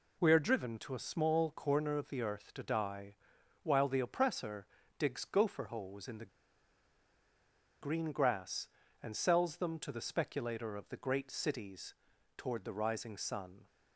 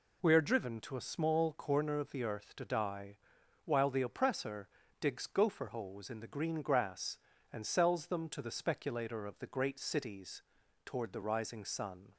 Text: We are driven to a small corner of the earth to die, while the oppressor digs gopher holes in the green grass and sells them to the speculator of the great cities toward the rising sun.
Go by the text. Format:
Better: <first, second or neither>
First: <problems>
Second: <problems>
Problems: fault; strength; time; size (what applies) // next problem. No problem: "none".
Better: second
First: pauses between "oppressor" and "digs"; slight; at 4.6 s; 0.32 s long // pauses between "the" and "green"; strong; at 6.2 s; 1.5 s long // pauses between "cities" and "toward"; at 11.9 s; 0.42 s long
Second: pauses between "oppressor" and "digs"; slight; at 4.6 s; 0.32 s long // pauses between "cities" and "toward"; at 10.4 s; 0.42 s long